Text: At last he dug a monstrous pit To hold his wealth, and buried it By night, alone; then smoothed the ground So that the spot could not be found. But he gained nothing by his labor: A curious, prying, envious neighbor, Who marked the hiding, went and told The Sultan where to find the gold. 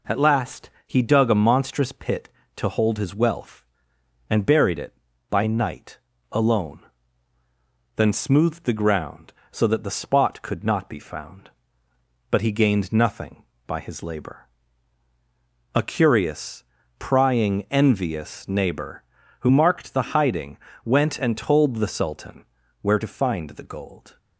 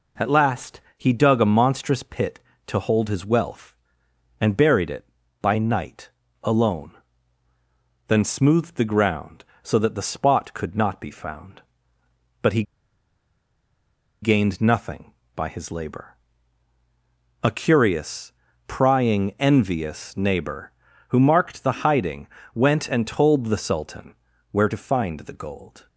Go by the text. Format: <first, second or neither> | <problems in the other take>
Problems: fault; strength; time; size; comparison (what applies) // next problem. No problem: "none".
first | pauses between "last" and "he"; slight; at 0.8 s; 0.16 s long; slight in the first // pauses between "he" and "gained"; strong; at 12.6 s; 1.5 s long // pauses between "Sultan" and "where"; at 24.1 s; 0.38 s long; also in the first